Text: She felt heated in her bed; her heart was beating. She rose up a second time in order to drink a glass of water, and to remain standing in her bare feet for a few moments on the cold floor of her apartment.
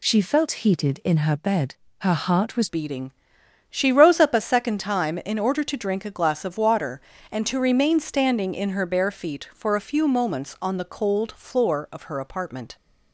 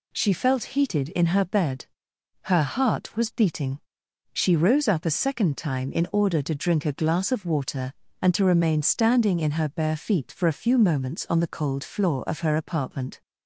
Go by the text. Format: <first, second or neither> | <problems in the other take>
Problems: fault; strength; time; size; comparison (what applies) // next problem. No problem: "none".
second | changes voice at "beating"; from 2.6 s on; 10.1 s long